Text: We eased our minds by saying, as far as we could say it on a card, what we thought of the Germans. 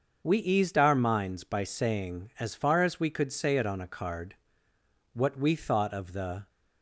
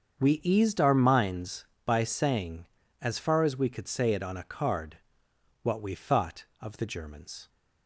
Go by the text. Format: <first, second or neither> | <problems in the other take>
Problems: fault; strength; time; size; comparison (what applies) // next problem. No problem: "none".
second | starts louder than the rest; until 1.2 s; 6.5 dB; strong in the second // stops before "Germans"; at 6.4 s